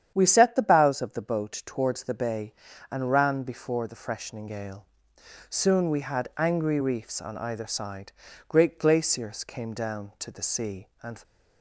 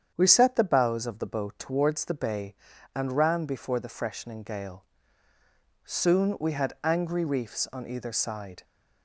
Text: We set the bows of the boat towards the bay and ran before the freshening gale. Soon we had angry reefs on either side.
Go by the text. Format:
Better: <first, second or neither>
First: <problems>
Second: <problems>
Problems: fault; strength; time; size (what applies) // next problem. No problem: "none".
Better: second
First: starts louder than the rest; strong; until 1.1 s; 9 dB // goes on to say "Great glaciers came down to the sea and"; strong; from 8.4 s on; 2.7 s long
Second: starts louder than the rest; strong; until 1.1 s; 8.5 dB